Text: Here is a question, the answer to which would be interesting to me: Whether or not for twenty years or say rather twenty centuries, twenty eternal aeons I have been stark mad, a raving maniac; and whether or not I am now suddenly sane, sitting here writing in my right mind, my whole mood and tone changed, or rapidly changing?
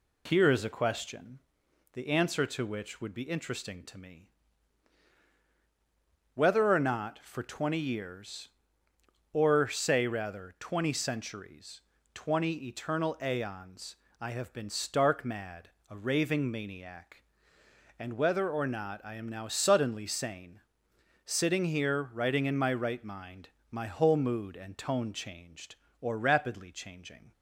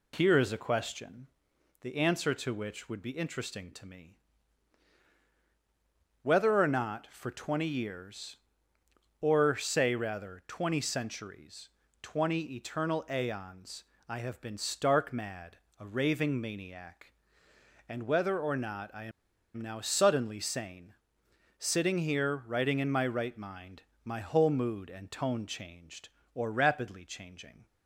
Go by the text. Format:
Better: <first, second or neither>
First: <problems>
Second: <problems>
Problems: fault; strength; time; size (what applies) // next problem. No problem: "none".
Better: first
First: pauses between "aeons" and "I"; slight; at 13.9 s; 0.26 s long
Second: pauses between "aeons" and "I"; slight; at 13.8 s; 0.26 s long // pauses between "I" and "am"; noticeable; at 19.0 s; 0.51 s long